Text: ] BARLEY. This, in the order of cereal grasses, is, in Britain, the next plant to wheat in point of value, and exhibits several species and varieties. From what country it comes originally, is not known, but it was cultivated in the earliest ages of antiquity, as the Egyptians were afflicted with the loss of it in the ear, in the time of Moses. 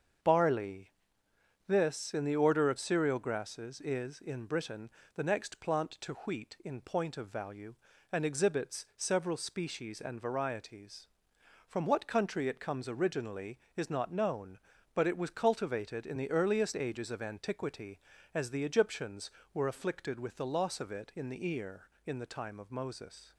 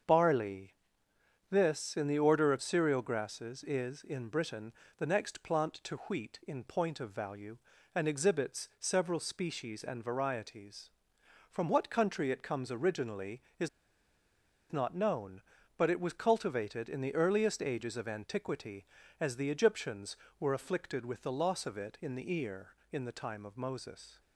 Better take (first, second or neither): first